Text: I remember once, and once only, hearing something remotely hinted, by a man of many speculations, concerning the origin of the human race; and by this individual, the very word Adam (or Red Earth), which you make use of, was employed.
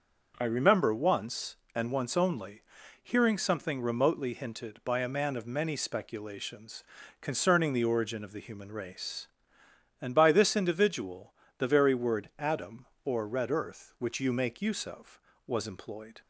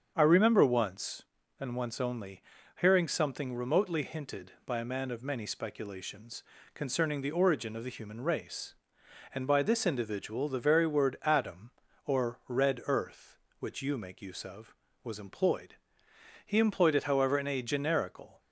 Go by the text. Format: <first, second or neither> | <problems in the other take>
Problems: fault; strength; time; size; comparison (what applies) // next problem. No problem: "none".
first | starts louder than the rest; until 1.1 s; 7 dB; noticeable in the first // goes on to say "He employed it however in a generical"; strong; from 16.4 s on; 1.9 s long